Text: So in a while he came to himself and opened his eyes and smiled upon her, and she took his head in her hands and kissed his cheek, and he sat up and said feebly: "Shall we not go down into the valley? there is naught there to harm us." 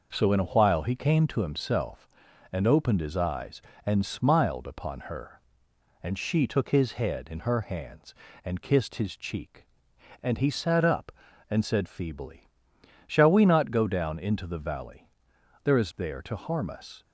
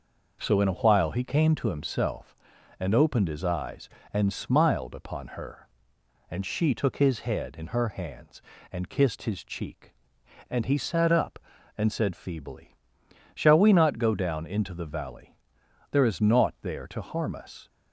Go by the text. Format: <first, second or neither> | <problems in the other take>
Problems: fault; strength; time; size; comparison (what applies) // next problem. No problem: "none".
second | skips "naught"; at 15.9 s